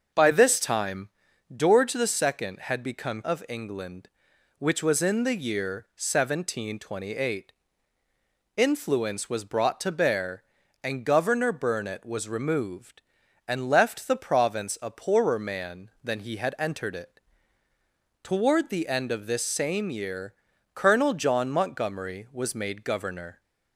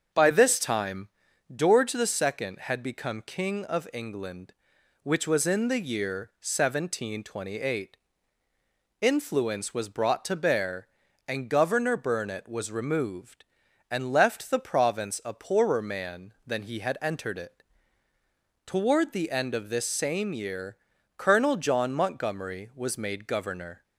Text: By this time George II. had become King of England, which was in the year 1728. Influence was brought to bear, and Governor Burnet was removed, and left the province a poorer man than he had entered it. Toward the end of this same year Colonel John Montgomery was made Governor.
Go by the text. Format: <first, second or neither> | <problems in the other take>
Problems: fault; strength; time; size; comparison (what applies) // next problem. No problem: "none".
second | starts louder than the rest; until 1.6 s; 6 dB; also in the second // pauses between "time" and "George"; noticeable; at 1.0 s; 0.46 s long; noticeable in the second // skips "King"; at 3.2 s // pauses between "year" and "Colonel"; at 20.3 s; 0.40 s long; also in the second